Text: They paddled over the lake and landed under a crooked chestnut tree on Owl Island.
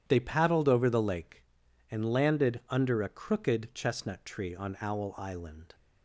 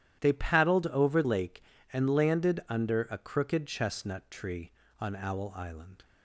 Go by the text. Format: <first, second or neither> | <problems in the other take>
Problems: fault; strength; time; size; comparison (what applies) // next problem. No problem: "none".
first | starts louder than the rest; strong; until 1.2 s; 11.5 dB; strong in the first // skips "the"; at 1.2 s